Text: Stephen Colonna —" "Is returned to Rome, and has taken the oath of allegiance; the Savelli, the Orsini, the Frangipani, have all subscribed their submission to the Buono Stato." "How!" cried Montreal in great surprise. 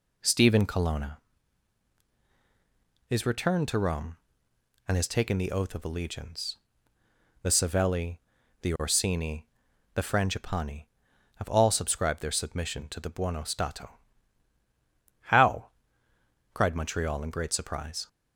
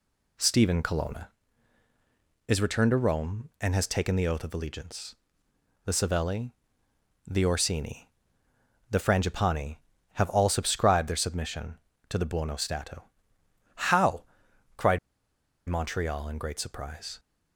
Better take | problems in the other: first | pauses between "cried" and "Montreal"; noticeable; at 14.9 s; 0.70 s long

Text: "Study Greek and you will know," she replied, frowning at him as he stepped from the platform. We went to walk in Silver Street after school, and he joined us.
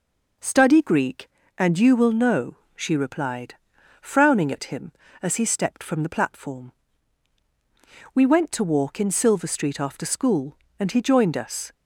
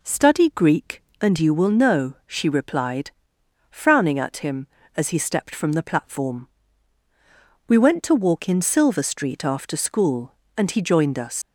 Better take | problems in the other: first | leaves "us" unfinished; at 11.4 s; 125 ms

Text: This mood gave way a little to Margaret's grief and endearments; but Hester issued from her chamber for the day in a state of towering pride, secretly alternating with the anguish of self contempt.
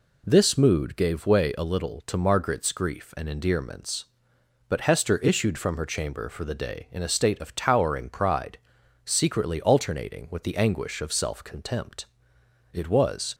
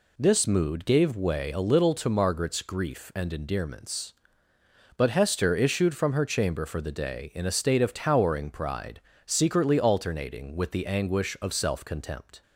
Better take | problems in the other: second | goes on to say "It was"; noticeable; from 12.7 s on; 0.62 s long

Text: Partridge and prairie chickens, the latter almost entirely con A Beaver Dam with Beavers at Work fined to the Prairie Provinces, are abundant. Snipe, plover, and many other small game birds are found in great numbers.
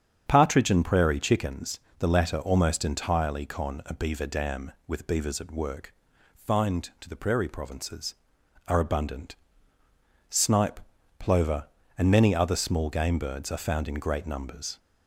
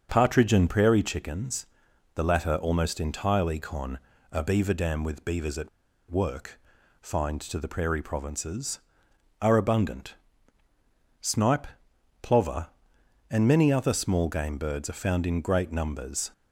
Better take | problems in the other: first | starts louder than the rest; until 1.1 s; 6.5 dB; strong in the first // pauses between "con" and "A"; slight; at 4.0 s; 0.32 s long // pauses between "at" and "Work"; at 5.6 s; 0.42 s long // pauses between "Work" and "fined"; at 6.5 s; 0.44 s long; also in the first

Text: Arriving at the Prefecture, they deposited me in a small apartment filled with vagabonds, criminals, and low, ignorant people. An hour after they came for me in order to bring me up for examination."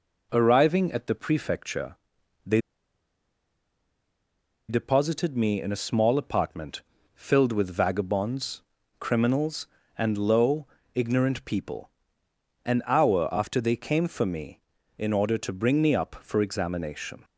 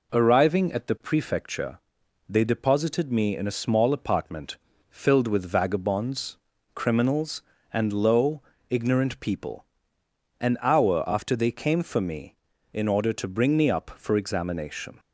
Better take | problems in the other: second | pauses between "they" and "deposited"; strong; at 2.6 s; 2.0 s long // pauses between "apartment" and "filled"; slight; at 6.8 s; 0.32 s long; slight in the second

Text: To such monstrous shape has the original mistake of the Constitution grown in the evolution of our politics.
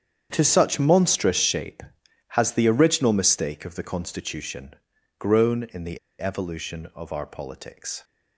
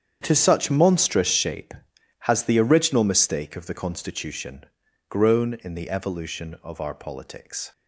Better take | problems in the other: second | starts louder than the rest; strong; until 1.3 s; 8.5 dB; strong in the second // pauses between "Constitution" and "grown"; noticeable; at 4.7 s; 0.46 s long; noticeable in the second // pauses between "the" and "evolution"; slight; at 5.9 s; 0.20 s long

